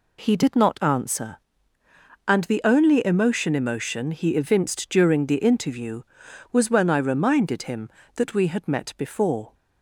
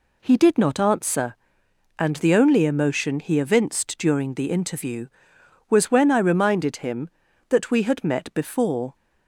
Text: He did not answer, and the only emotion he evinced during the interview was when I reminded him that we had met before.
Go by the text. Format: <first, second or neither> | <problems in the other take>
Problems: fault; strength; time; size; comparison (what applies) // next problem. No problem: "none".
second | says "emotion" twice; at 3.5 s